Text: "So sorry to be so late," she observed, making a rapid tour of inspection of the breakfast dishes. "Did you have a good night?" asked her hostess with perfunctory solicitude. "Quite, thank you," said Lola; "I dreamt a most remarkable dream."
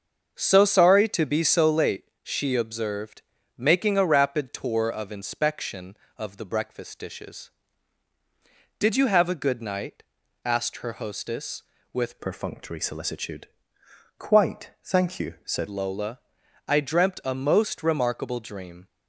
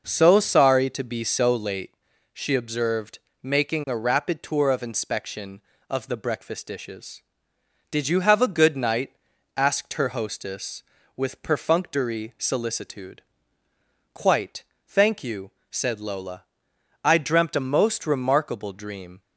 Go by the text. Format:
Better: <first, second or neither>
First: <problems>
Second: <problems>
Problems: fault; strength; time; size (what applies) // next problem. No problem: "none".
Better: second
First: starts louder than the rest; until 1.3 s; 6.5 dB // changes voice from "perfunctory" to "said"; from 12.2 to 15.6 s; 3.4 s long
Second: none